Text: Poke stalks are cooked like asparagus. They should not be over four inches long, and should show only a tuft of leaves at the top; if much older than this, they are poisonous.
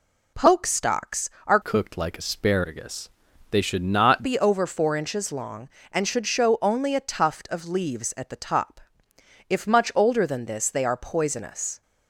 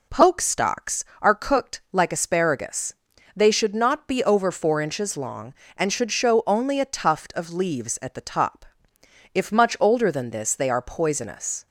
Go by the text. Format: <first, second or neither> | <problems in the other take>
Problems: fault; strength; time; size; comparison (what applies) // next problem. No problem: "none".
second | changes voice from "cooked" to "not"; from 1.6 to 4.2 s; 2.6 s long